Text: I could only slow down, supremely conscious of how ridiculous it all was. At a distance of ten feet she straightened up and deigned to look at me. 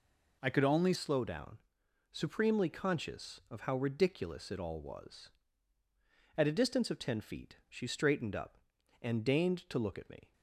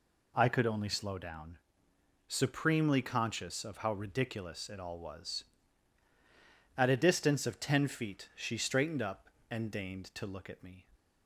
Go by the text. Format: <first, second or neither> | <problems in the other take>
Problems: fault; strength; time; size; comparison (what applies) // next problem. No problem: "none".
second | changes voice at "slow"; from 0.9 s on; 9.4 s long